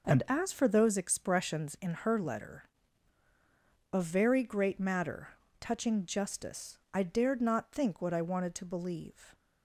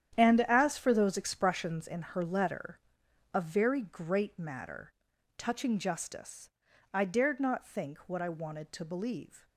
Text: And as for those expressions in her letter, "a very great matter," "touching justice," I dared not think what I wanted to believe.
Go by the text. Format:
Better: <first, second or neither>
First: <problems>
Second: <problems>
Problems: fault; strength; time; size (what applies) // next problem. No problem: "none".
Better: first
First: none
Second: gets quieter; strong; throughout; 11.5 dB